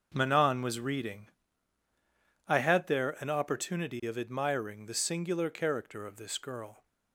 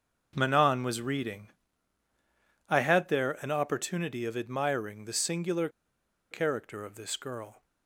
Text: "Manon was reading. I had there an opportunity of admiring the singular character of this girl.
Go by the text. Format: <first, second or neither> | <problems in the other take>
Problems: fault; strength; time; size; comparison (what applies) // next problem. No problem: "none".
first | starts louder than the rest; until 1.3 s; 6.5 dB; also in the first // pauses between "singular" and "character"; noticeable; at 5.6 s; 0.62 s long